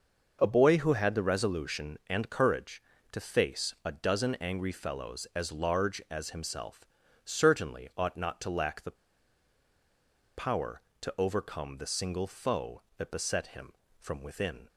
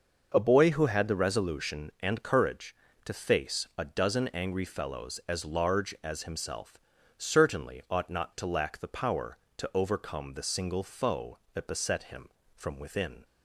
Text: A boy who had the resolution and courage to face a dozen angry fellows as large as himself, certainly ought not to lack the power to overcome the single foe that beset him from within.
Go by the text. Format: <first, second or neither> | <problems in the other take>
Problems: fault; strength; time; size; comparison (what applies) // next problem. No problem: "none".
second | starts louder than the rest; noticeable; until 1.4 s; 6 dB; noticeable in the second // pauses between "the" and "power"; strong; at 8.9 s; 1.4 s long